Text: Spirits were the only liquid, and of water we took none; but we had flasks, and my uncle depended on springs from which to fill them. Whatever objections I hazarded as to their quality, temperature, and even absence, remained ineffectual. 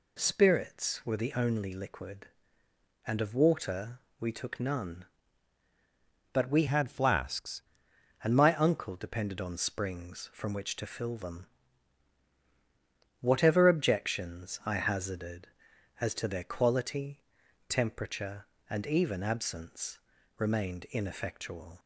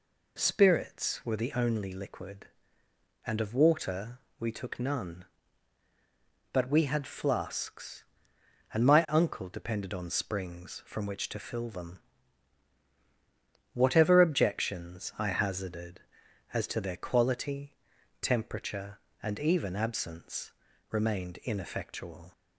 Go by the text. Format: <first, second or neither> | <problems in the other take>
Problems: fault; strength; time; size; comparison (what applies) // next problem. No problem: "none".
second | pauses between "water" and "we"; slight; at 3.9 s; 0.20 s long; slight in the second // changes voice from "had" to "flasks"; from 6.6 to 7.6 s; 1.0 s long